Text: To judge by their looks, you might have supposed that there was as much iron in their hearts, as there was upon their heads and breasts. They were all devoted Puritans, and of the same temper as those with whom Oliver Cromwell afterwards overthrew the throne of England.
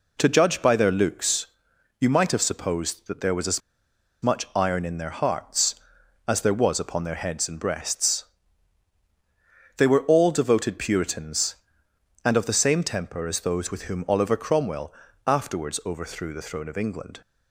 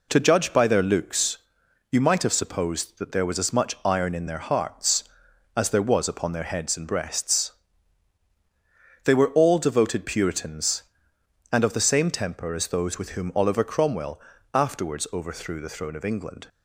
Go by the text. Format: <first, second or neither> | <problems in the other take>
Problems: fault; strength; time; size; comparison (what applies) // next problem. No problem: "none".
second | pauses between "as" and "much"; noticeable; at 3.6 s; 0.62 s long // pauses between "Cromwell" and "afterwards"; slight; at 14.9 s; 0.32 s long; slight in the second